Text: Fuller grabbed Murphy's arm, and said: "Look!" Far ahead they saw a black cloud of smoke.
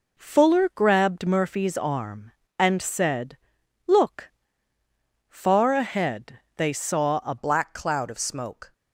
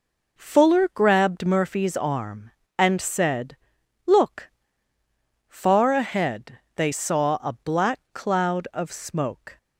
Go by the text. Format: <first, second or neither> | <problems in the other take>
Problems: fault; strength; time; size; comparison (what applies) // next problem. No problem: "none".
second | pauses between "ahead" and "they"; slight; at 6.3 s; 0.16 s long; slight in the second // changes voice at "black"; from 7.3 s on; 1.4 s long